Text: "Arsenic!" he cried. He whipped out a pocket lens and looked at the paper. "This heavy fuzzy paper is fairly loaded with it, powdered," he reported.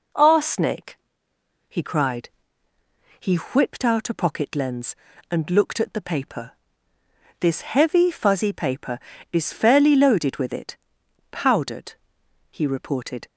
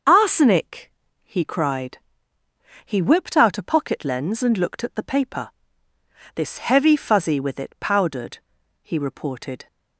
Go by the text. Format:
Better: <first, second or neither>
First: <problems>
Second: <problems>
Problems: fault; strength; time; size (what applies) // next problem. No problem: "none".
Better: first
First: none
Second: starts louder than the rest; until 1.3 s; 6.5 dB // skips "paper is fairly loaded"; at 7.3 s